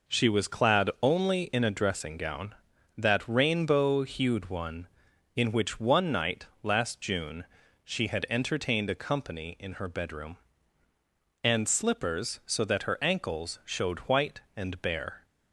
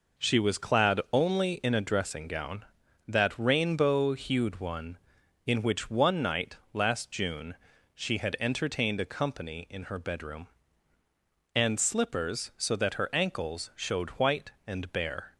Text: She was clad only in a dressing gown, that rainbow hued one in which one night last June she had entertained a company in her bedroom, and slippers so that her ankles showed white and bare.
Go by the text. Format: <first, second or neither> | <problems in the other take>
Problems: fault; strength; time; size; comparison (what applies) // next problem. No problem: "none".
neither | pauses between "night" and "last"; slight; the same in both // pauses between "June" and "she"; the same in both